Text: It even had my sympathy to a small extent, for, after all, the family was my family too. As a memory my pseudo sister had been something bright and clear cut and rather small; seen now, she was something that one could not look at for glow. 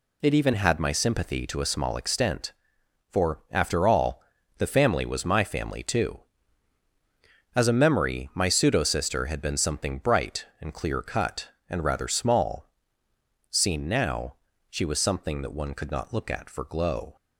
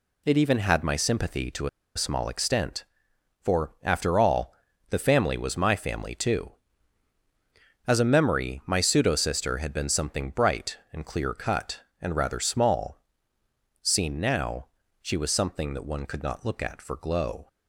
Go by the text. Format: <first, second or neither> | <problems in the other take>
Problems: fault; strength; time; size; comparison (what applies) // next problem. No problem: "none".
first | pauses between "to" and "a"; slight; at 1.6 s; 0.28 s long